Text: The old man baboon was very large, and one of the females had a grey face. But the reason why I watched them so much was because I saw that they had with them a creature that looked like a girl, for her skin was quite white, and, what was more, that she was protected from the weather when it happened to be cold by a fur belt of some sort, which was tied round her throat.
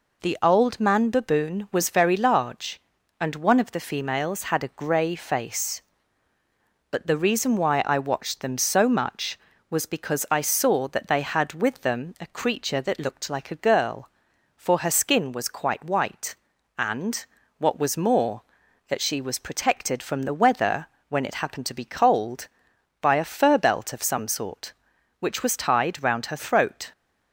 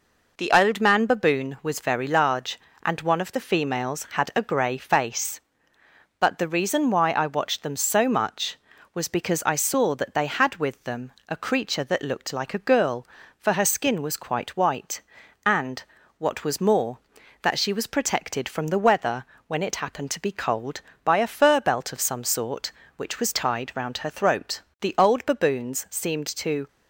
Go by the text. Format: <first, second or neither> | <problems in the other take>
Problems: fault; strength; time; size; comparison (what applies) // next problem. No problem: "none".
first | pauses between "them" and "a"; slight; at 11.1 s; 0.18 s long // pauses between "weather" and "when"; slight; at 19.2 s; 0.24 s long; slight in the first // goes on to say "The old baboons seemed to"; strong; from 24.8 s on; 1.8 s long